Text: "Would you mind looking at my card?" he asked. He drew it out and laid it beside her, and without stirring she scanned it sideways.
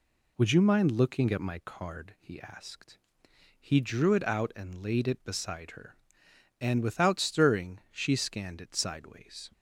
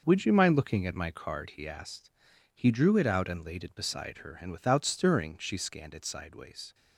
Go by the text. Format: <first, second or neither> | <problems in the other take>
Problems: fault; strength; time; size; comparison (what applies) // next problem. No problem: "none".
first | gets quieter; strong; throughout; 9.5 dB